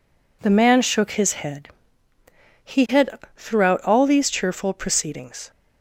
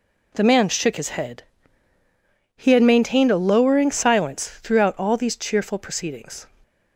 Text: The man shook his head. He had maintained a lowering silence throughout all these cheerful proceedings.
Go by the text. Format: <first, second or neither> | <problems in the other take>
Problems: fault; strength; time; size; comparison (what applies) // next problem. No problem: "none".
second | skips "maintained a lowering silence"; at 3.2 s